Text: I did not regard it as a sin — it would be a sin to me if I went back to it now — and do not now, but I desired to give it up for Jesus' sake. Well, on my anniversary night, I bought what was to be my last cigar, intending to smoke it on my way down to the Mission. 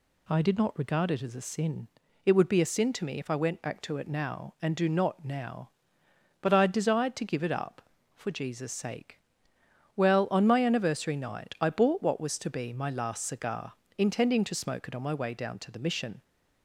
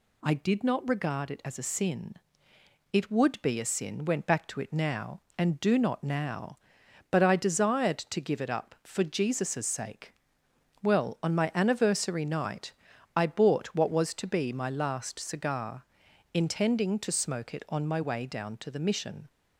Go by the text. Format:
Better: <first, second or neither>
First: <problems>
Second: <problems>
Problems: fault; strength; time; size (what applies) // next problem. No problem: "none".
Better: first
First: none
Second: skips "to me if I"; at 4.0 s